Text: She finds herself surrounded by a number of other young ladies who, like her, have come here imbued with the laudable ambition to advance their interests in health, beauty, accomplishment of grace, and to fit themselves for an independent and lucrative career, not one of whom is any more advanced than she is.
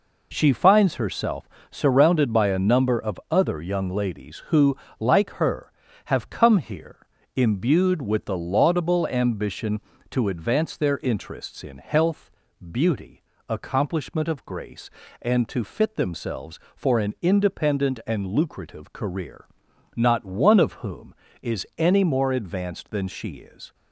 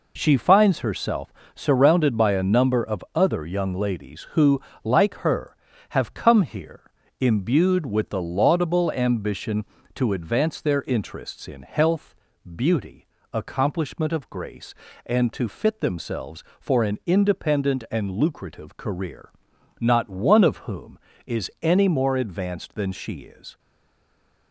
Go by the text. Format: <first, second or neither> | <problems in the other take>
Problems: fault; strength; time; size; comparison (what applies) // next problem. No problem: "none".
first | pauses between "herself" and "surrounded"; slight; at 1.3 s; 0.24 s long; slight in the first // pauses between "here" and "imbued"; slight; at 6.8 s; 0.32 s long; slight in the first // stays silent after the last word; slight; from 23.5 s on; 1.0 s long